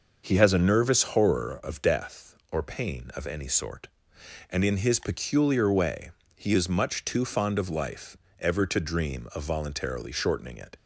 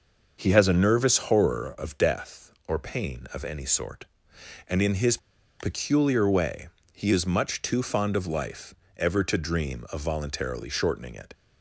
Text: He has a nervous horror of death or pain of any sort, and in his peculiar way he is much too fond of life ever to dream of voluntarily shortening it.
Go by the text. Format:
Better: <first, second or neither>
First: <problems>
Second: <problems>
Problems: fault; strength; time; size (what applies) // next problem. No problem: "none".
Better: first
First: starts louder than the rest; until 1.3 s; 6.5 dB // pauses between "way" and "he"; slight; at 6.1 s; 0.24 s long // pauses between "life" and "ever"; slight; at 8.1 s; 0.22 s long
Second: starts louder than the rest; until 1.4 s; 6.5 dB // pauses between "his" and "peculiar"; at 5.1 s; 0.42 s long // pauses between "way" and "he"; slight; at 6.6 s; 0.24 s long // pauses between "life" and "ever"; slight; at 8.7 s; 0.22 s long